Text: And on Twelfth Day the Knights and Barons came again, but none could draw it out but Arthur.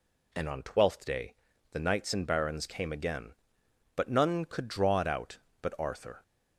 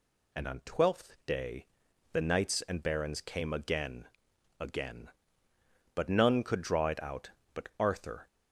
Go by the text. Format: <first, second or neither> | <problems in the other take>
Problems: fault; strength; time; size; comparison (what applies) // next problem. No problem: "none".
first | pauses between "Day" and "the"; noticeable; at 1.6 s; 0.48 s long; also in the first // says "again" twice; at 4.5 s